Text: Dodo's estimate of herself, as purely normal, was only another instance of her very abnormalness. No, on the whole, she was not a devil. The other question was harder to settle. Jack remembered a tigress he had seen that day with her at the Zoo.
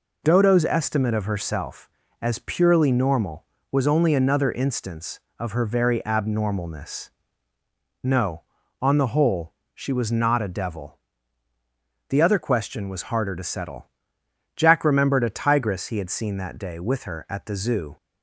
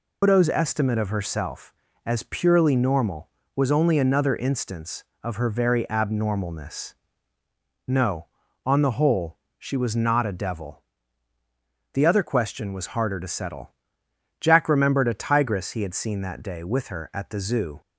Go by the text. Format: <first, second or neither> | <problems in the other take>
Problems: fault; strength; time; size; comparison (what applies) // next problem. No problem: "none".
first | loses the start of "Dodo's"; at 0.2 s; 140 ms